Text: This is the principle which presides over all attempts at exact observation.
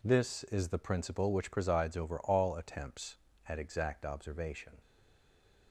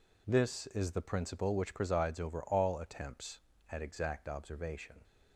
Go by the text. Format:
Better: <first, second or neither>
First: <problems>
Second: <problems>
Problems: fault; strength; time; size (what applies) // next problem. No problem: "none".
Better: second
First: stays silent after the last word; slight; from 4.8 s on; 0.9 s long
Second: none